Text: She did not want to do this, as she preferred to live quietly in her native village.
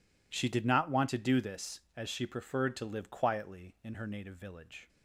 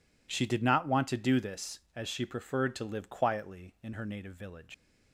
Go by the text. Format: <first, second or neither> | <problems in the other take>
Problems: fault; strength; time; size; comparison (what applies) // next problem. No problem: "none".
first | leaves "village" unfinished; at 4.7 s; 120 ms